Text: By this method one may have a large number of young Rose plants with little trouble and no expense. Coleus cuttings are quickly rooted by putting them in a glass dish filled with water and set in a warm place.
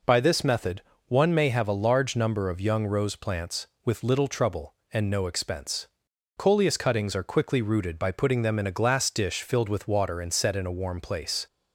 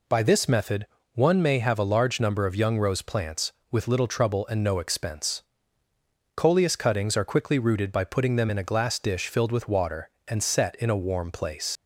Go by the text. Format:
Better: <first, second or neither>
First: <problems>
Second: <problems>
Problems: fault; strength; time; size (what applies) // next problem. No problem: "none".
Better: first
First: pauses between "method" and "one"; slight; at 0.8 s; 0.26 s long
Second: pauses between "method" and "one"; slight; at 0.8 s; 0.28 s long // leaves "place" unfinished; at 11.7 s; 85 ms